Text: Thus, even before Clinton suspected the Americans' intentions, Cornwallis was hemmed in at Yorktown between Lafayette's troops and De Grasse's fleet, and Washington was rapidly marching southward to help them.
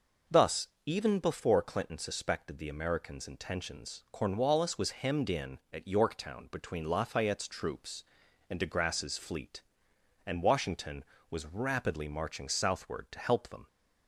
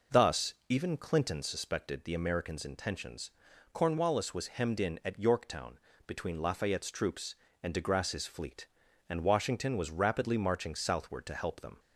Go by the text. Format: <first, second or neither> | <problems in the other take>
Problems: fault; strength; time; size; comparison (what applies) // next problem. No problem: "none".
first | skips "before"; at 0.9 s // pauses between "Yorktown" and "between"; slight; at 5.7 s; 0.30 s long